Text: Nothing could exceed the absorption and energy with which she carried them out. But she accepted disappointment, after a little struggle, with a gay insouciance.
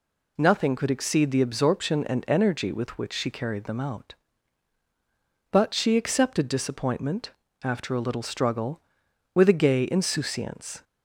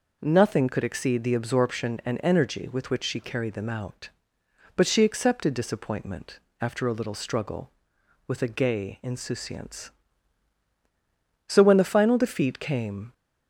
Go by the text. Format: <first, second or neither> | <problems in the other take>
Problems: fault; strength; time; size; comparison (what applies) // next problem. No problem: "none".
first | goes on to say "So when the final defeat came"; from 11.4 s on; 1.6 s long